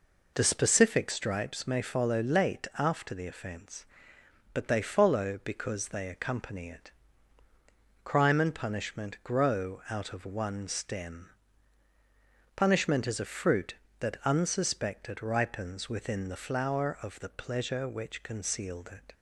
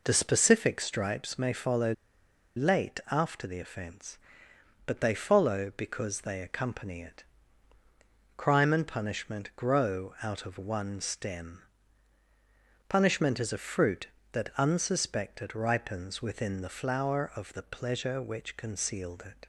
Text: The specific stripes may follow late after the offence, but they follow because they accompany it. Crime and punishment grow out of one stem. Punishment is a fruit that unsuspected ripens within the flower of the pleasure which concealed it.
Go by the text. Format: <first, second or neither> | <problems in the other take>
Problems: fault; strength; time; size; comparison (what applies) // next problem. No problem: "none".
first | pauses between "follow" and "late"; noticeable; at 1.9 s; 0.63 s long